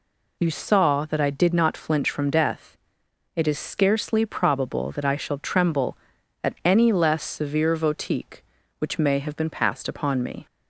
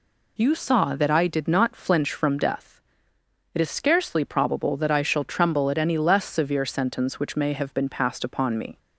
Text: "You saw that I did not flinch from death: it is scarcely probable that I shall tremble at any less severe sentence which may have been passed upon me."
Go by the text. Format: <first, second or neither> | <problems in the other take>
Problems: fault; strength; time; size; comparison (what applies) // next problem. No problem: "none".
second | says "votique" for "sentence"; at 7.7 s